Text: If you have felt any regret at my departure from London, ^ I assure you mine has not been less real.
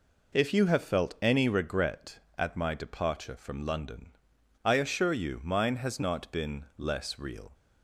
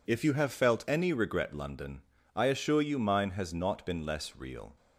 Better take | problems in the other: first | skips "at my departure from"; at 1.5 s

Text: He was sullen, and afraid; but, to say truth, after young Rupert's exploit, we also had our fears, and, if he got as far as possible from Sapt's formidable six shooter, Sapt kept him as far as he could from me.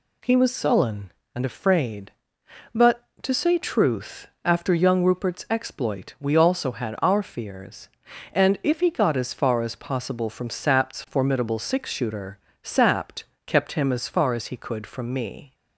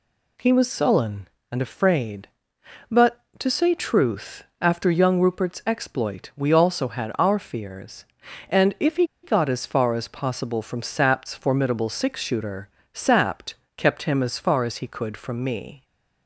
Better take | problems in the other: first | pauses between "he" and "got"; slight; at 9.0 s; 0.16 s long // pauses between "Sapt" and "kept"; slight; at 13.5 s; 0.24 s long; slight in the first

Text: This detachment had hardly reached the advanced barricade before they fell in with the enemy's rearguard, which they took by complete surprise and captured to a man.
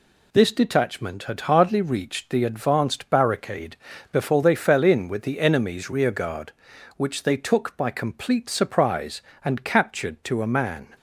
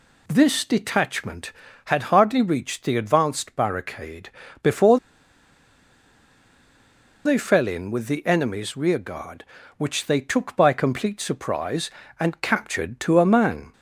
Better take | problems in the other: first | pauses between "barricade" and "before"; slight; at 4.2 s; 0.32 s long; slight in the first // pauses between "before" and "they"; strong; at 4.9 s; 2.2 s long

